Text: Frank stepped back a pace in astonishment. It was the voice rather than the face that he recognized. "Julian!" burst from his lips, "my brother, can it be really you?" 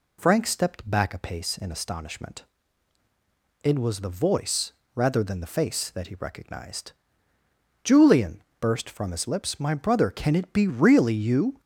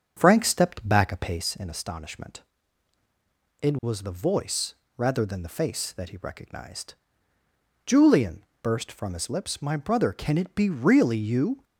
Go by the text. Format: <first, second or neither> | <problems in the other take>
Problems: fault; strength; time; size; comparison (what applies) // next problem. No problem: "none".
first | starts louder than the rest; strong; until 1.6 s; 7.5 dB // pauses between "voice" and "rather"; slight; at 4.7 s; 0.20 s long; slight in the first